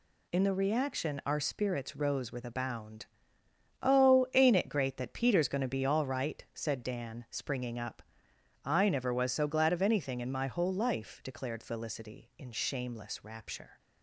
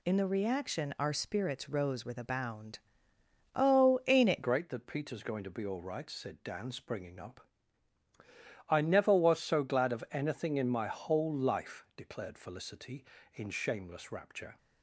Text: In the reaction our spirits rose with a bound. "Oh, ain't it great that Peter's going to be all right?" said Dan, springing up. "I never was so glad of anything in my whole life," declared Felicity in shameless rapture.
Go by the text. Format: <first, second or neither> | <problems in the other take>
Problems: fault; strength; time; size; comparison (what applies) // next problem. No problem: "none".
first | changes voice at "great"; from 4.4 s on; 10.1 s long